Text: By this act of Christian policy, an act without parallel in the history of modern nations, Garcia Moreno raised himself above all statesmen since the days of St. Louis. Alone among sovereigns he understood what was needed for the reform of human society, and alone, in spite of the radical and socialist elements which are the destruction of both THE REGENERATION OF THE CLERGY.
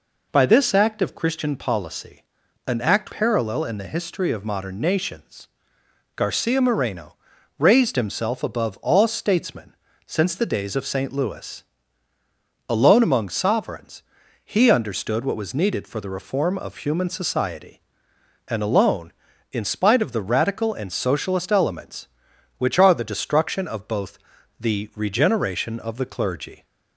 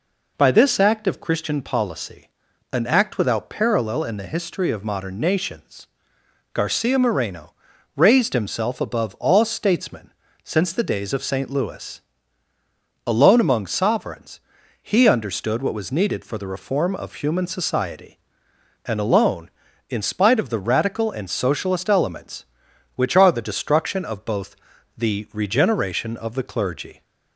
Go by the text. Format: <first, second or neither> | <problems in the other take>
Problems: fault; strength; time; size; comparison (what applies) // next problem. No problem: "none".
second | skips "without"; at 3.1 s // pauses between "Moreno" and "raised"; at 7.1 s; 0.44 s long; also in the second // pauses between "statesmen" and "since"; slight; at 9.7 s; 0.32 s long; slight in the second // pauses between "sovereigns" and "he"; at 14.0 s; 0.40 s long; also in the second // pauses between "both" and "THE"; at 24.1 s; 0.40 s long; also in the second